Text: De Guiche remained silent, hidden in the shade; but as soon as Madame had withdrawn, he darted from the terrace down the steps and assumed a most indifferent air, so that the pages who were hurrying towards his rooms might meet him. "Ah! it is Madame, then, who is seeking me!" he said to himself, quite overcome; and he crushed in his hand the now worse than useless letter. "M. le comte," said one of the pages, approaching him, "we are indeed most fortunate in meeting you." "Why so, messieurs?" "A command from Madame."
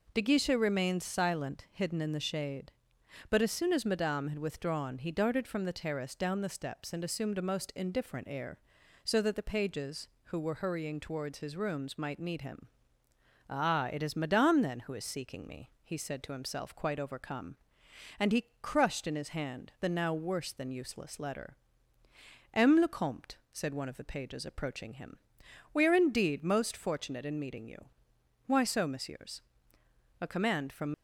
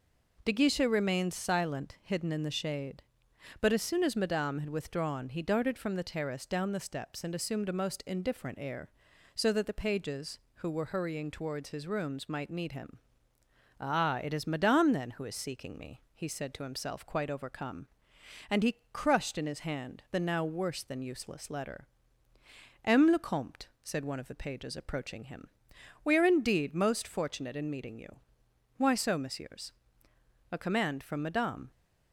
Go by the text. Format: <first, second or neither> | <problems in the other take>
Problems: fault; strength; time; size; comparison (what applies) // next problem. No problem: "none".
second | stops before "Madame"; at 30.9 s